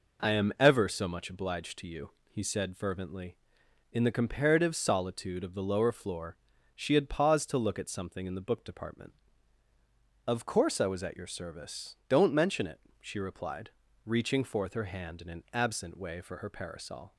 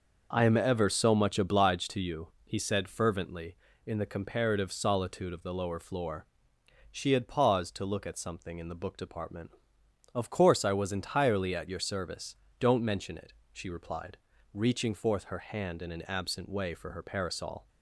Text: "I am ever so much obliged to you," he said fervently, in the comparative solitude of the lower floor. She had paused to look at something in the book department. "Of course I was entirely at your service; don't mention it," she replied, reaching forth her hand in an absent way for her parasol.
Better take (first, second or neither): second